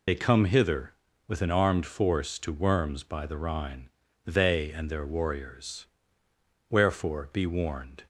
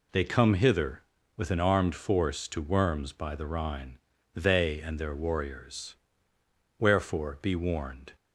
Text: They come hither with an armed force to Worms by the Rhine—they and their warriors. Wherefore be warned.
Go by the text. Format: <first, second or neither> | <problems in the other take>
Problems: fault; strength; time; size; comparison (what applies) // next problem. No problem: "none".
second | loses the start of "They"; at 0.0 s; 55 ms